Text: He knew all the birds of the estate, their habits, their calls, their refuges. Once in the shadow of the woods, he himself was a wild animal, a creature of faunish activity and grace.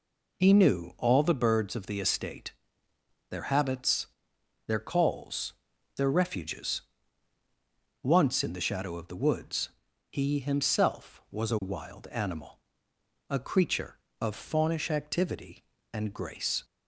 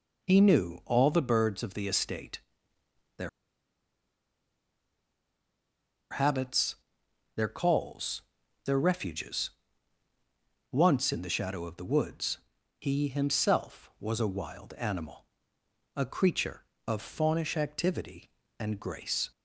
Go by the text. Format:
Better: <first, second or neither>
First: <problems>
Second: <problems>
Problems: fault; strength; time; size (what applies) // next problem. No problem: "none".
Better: first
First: none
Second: pauses between "their" and "habits"; strong; at 3.2 s; 2.8 s long